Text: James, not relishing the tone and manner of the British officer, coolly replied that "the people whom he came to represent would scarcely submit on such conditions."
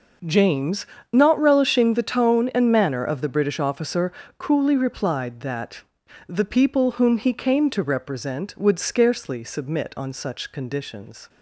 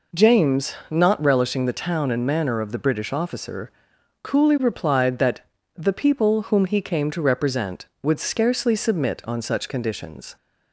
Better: first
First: pauses between "that" and "the"; at 5.8 s; 0.44 s long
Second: says "town" for "tone"; at 1.7 s // pauses between "that" and "the"; slight; at 5.4 s; 0.34 s long

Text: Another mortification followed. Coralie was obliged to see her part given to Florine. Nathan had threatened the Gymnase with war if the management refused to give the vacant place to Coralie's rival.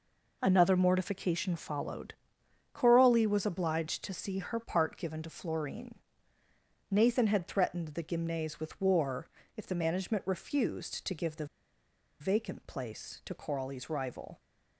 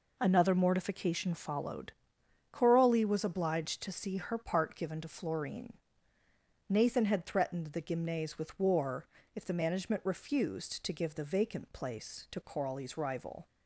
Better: second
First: pauses between "war" and "if"; slight; at 9.2 s; 0.28 s long // pauses between "the" and "vacant"; noticeable; at 11.4 s; 0.74 s long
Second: pauses between "war" and "if"; slight; at 9.0 s; 0.28 s long

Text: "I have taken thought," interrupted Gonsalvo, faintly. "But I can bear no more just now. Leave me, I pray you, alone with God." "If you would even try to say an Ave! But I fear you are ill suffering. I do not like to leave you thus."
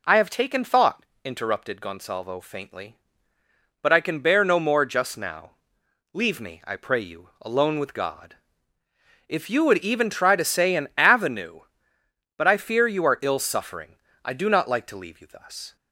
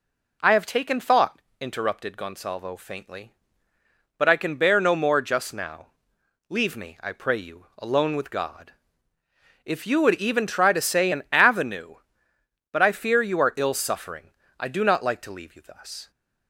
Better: neither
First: none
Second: none

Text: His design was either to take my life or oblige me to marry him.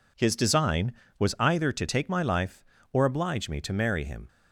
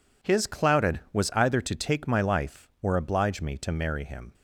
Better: first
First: none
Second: says "clouded" for "design"; at 0.4 s

